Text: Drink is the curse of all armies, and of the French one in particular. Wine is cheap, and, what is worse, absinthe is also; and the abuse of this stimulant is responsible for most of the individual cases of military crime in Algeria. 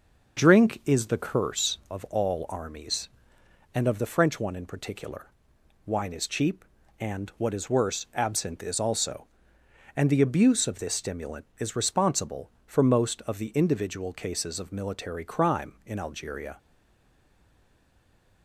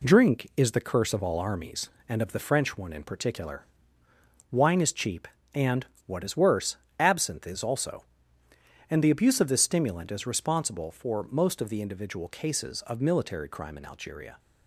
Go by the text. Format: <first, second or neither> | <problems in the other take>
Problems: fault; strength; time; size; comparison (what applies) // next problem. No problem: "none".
second | starts louder than the rest; until 1.4 s; 6 dB // stays silent after the last word; noticeable; from 16.5 s on; 1.9 s long